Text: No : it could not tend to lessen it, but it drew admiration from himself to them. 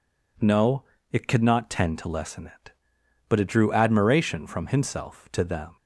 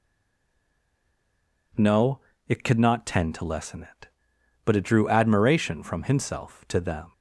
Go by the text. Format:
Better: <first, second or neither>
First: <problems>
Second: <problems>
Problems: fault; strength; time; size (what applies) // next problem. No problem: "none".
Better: first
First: none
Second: stays silent before the first word; noticeable; until 1.7 s; 1.7 s long